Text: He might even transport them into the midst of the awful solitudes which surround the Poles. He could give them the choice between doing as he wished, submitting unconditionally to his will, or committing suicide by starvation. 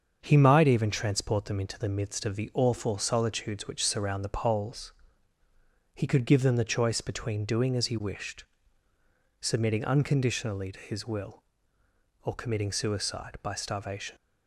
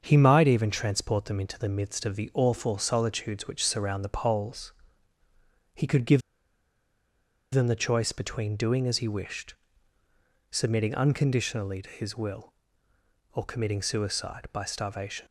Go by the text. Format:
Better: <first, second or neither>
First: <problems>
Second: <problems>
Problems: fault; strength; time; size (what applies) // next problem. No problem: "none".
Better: first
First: starts louder than the rest; until 1.2 s; 7 dB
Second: starts louder than the rest; until 1.0 s; 7 dB // pauses between "give" and "them"; strong; at 6.2 s; 1.3 s long